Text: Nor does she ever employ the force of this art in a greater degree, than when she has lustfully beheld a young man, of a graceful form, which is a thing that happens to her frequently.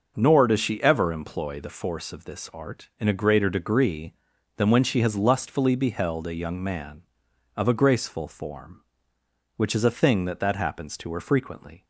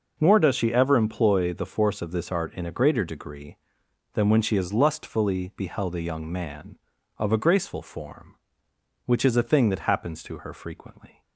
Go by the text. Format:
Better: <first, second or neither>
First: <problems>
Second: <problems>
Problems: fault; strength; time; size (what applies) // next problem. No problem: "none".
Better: second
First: says "that" twice; at 10.3 s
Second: none